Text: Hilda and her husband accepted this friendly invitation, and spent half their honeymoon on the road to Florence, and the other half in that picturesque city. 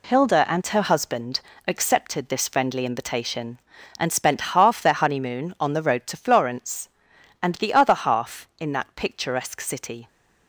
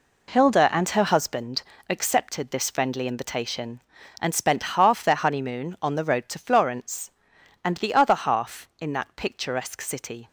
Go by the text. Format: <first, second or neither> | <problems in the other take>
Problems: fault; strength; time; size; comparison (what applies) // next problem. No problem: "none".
first | starts louder than the rest; slight; until 1.3 s; 3.5 dB // pauses between "husband" and "accepted"; slight; at 1.6 s; 0.26 s long; slight in the first